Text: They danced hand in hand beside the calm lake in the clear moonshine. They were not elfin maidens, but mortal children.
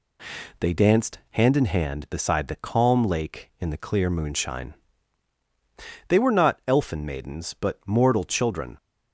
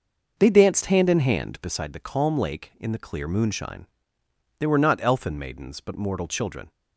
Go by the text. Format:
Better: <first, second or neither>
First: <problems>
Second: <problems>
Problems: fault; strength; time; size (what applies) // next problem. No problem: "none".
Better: first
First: none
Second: starts louder than the rest; noticeable; until 1.9 s; 6 dB